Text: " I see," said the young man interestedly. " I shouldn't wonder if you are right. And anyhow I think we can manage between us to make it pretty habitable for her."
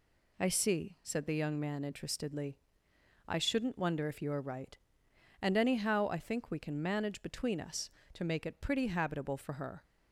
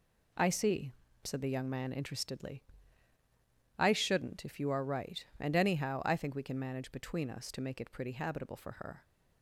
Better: first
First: none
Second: skips "wonder"; at 4.4 s

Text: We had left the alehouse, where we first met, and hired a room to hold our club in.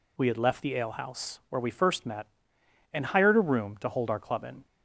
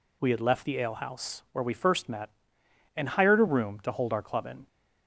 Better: neither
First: none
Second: none

